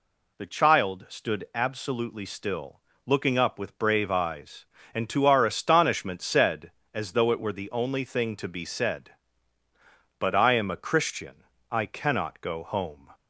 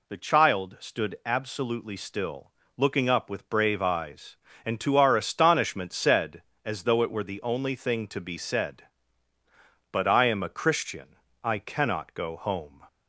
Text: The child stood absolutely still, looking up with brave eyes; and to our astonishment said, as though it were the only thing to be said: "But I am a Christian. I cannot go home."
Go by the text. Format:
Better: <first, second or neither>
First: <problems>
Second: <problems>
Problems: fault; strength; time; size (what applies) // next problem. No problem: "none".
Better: neither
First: none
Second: none